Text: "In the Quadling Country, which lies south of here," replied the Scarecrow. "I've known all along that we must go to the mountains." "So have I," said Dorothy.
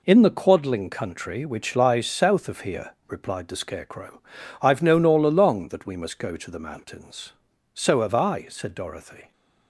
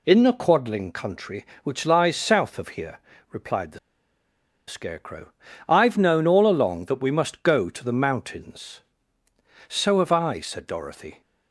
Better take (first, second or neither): first